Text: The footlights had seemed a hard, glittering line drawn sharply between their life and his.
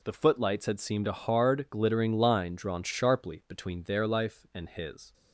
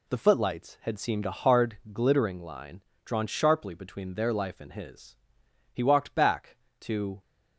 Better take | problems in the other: first | pauses between "line" and "drawn"; slight; at 2.8 s; 0.22 s long // goes on to say "He walked back to"; from 5.7 s on; 1.4 s long

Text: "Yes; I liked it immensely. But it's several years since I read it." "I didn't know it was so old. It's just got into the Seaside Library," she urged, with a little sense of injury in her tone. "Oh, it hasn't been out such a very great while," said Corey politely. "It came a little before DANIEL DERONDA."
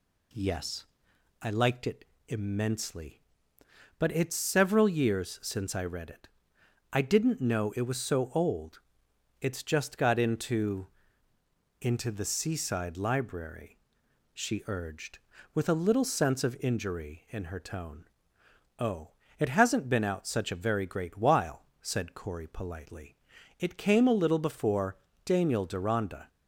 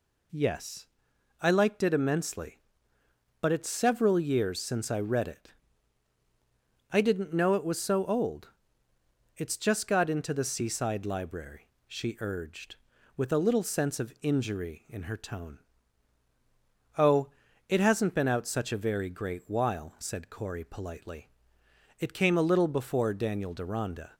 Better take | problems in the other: second | pauses between "it" and "immensely"; slight; at 2.0 s; 0.24 s long // says "into" twice; at 11.8 s // pauses between "before" and "DANIEL"; slight; at 24.9 s; 0.28 s long

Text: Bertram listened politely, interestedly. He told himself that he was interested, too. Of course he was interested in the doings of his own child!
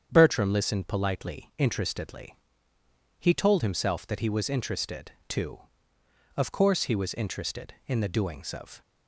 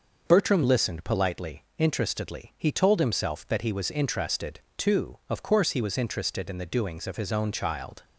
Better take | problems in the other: second | starts louder than the rest; strong; until 1.1 s; 8 dB // stops before "his own child"; at 8.8 s

